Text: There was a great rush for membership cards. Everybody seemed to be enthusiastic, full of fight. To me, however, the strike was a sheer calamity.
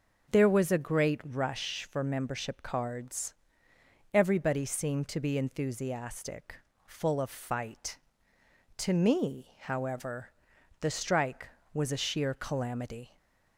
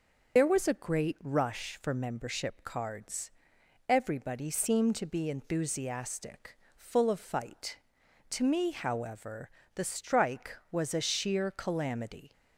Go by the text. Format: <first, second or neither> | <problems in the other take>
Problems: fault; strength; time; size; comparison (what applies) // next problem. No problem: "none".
first | loses the start of "There"; at 0.3 s; 55 ms // starts louder than the rest; noticeable; until 1.4 s; 6 dB